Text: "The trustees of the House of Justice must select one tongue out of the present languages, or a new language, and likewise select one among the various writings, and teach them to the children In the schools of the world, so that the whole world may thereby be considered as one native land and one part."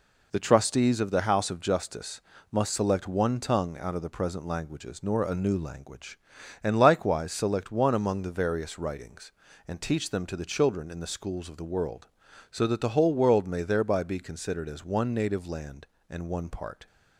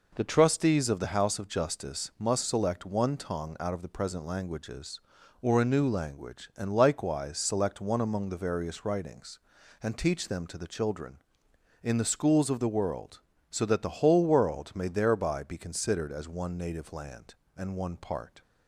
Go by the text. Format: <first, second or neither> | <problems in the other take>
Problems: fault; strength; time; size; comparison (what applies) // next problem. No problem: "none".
second | pauses between "Justice" and "must"; slight; at 2.1 s; 0.32 s long // says "nor" for "or"; at 5.0 s